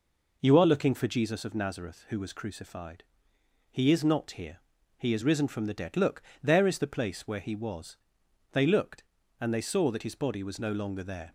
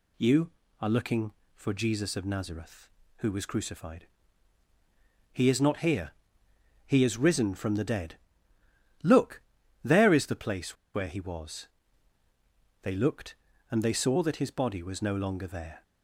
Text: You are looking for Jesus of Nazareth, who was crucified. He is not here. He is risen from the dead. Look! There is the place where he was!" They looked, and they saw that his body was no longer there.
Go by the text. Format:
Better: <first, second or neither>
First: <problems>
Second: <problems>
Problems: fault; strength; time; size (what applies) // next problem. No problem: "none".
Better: first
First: none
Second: pauses between "place" and "where"; slight; at 10.7 s; 0.18 s long